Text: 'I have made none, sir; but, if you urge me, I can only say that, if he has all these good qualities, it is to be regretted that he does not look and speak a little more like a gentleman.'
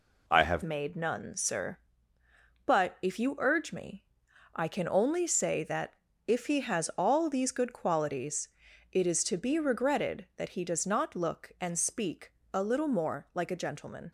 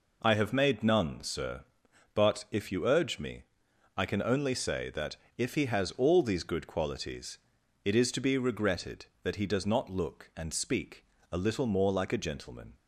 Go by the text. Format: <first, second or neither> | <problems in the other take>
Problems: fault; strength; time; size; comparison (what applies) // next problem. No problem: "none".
second | changes voice at "made"; from 0.6 s on; 13.5 s long // pauses between "speak" and "a"; slight; at 12.3 s; 0.20 s long; slight in the second